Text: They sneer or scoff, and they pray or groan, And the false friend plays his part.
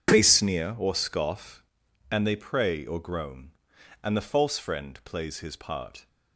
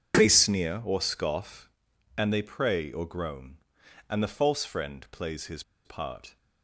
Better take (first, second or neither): first